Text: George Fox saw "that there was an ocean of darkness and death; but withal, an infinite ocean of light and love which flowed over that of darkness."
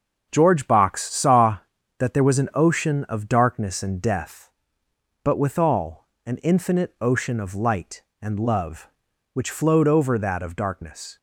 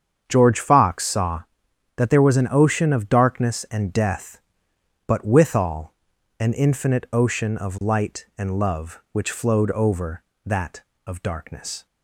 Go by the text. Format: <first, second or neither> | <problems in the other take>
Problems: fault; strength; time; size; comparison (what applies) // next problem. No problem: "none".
second | starts louder than the rest; until 1.3 s; 6.5 dB; strong in the second // says "Box" for "Fox"; at 0.6 s